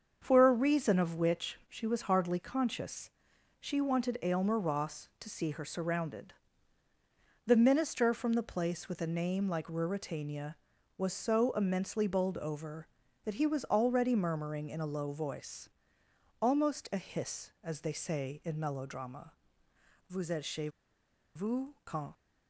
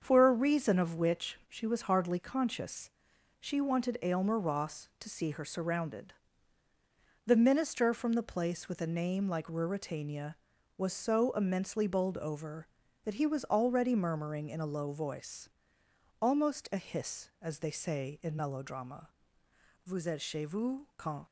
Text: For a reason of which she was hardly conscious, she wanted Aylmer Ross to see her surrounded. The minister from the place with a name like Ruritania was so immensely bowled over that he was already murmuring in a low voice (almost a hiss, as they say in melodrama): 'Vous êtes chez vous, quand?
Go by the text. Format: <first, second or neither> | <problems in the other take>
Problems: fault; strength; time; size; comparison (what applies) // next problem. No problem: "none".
second | starts louder than the rest; until 1.2 s; 6.5 dB; also in the second // pauses between "chez" and "vous"; noticeable; at 20.6 s; 0.66 s long